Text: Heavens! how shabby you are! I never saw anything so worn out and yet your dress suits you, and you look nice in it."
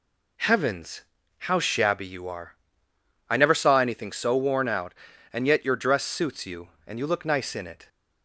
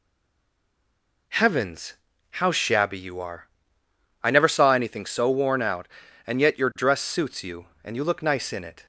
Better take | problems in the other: first | stays silent before the first word; noticeable; until 1.2 s; 1.2 s long

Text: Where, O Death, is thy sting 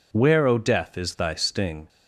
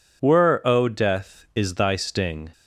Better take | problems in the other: first | says "Were" for "Where"; at 0.2 s

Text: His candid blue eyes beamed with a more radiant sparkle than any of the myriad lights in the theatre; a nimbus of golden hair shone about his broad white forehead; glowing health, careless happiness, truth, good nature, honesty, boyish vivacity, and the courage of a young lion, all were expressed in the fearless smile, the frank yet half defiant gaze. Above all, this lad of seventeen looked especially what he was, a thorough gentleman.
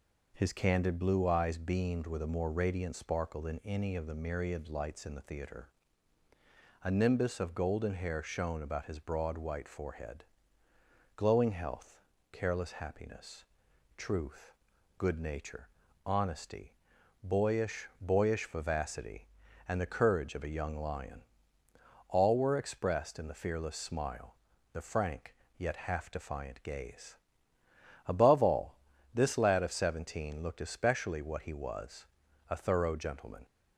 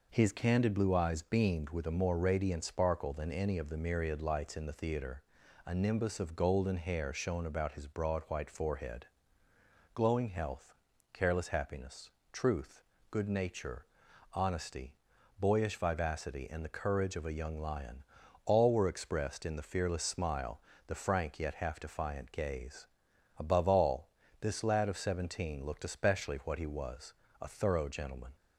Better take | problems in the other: second | says "boyish" twice; at 18.0 s // pauses between "frank" and "yet"; slight; at 25.3 s; 0.24 s long

